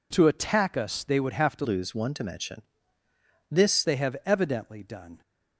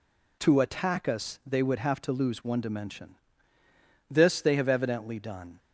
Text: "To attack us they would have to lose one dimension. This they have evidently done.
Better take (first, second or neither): second